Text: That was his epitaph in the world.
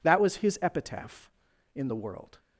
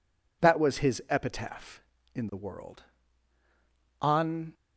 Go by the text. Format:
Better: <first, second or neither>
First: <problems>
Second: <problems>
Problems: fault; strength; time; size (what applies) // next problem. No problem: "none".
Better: first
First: none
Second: goes on to say "On"; from 4.0 s on; 0.52 s long